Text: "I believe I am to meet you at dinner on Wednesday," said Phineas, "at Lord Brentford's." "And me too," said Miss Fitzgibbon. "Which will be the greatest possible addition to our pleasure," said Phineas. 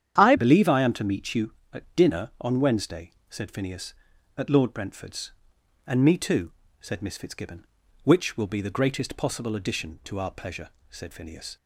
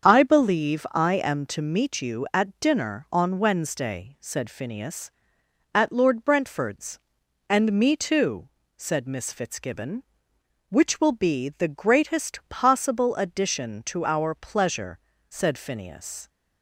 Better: second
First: starts louder than the rest; strong; until 1.2 s; 9 dB // changes voice at "believe"; from 0.3 s on; 11.2 s long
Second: starts louder than the rest; strong; until 1.1 s; 7 dB

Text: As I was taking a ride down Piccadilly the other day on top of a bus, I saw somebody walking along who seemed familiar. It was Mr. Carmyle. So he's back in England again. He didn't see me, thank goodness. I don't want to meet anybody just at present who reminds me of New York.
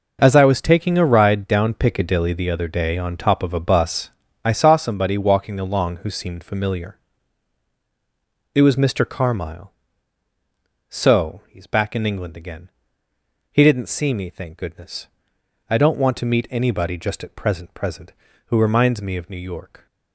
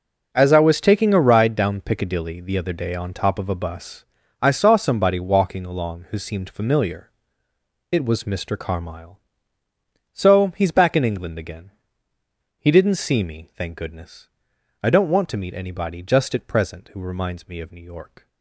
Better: second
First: says "present" twice; at 17.7 s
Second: none

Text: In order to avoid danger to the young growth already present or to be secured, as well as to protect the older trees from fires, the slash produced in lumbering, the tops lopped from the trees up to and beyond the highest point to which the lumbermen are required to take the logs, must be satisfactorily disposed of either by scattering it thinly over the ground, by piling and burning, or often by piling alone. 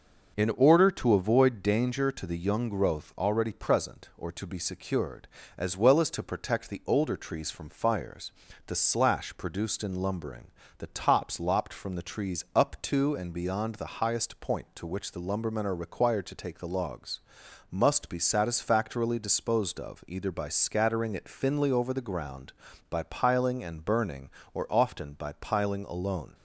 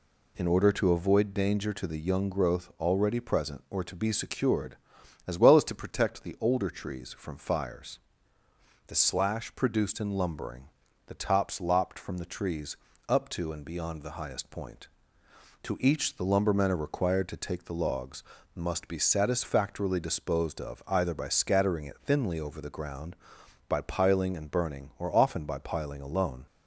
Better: first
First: none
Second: pauses between "trees" and "up"; slight; at 12.7 s; 0.32 s long // says "each" for "which"; at 15.7 s

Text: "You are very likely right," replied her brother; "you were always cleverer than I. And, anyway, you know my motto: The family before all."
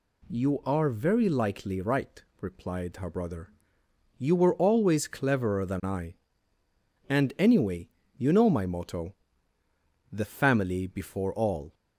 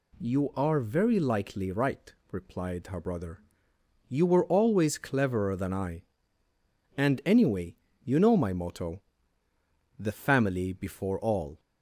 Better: neither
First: none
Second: none

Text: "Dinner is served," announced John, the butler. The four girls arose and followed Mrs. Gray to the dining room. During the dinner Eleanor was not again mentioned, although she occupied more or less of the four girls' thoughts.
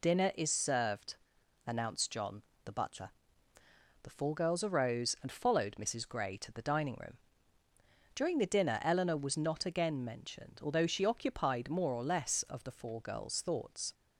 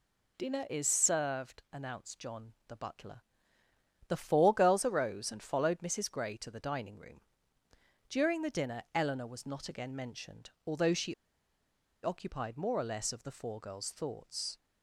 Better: first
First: none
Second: pauses between "she" and "occupied"; noticeable; at 11.1 s; 0.88 s long

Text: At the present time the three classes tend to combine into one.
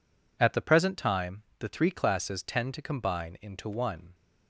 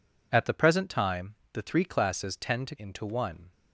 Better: first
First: pauses between "time" and "the"; slight; at 1.4 s; 0.16 s long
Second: pauses between "time" and "the"; slight; at 1.3 s; 0.18 s long // skips "combine"; at 2.7 s

